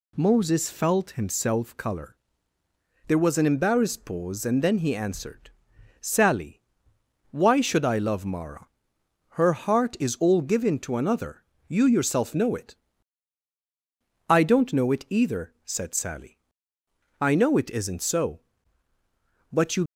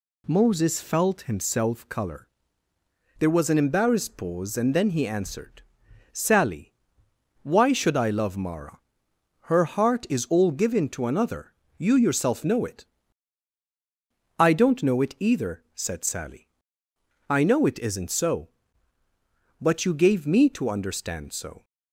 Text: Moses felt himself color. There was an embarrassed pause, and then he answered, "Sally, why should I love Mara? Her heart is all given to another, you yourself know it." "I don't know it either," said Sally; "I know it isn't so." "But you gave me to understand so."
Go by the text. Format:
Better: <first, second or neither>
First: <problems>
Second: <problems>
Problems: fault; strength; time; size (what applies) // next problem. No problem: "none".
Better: second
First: stops before "gave me to understand so"; at 19.8 s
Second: none